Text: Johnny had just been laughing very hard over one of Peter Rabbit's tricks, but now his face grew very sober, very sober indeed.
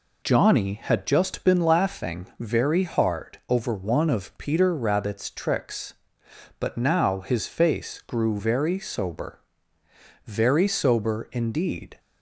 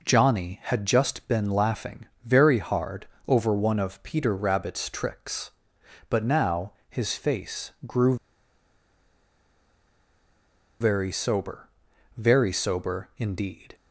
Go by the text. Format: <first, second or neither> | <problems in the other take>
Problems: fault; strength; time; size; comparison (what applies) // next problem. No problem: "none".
first | pauses between "laughing" and "very"; slight; at 2.0 s; 0.18 s long // pauses between "hard" and "over"; slight; at 3.0 s; 0.22 s long // pauses between "now" and "his"; slight; at 6.7 s; 0.18 s long // pauses between "face" and "grew"; slight; at 7.6 s; 0.16 s long // pauses between "grew" and "very"; strong; at 8.1 s; 2.6 s long